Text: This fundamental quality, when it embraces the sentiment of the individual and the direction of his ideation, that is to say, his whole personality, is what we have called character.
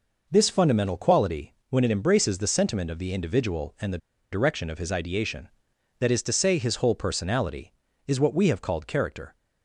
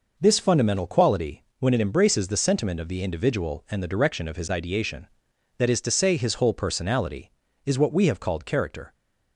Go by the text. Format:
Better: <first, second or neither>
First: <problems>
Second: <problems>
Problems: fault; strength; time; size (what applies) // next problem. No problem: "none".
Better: second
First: pauses between "the" and "direction"; slight; at 3.9 s; 0.34 s long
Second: none